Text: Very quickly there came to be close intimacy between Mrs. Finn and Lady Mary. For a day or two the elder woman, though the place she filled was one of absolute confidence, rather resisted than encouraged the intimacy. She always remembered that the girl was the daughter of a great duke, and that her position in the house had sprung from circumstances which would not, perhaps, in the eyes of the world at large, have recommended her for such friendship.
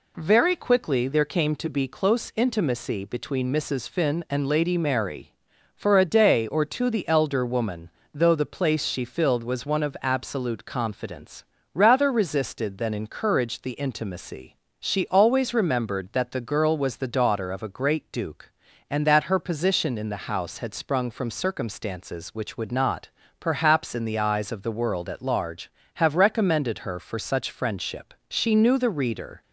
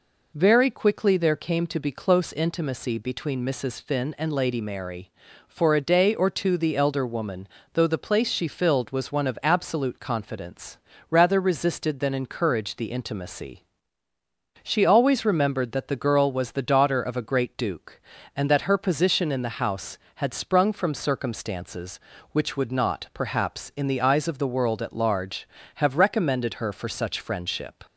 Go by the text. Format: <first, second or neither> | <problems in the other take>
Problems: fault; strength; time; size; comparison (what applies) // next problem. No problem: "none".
second | goes on to say "She knew the reader"; noticeable; from 28.2 s on; 1.1 s long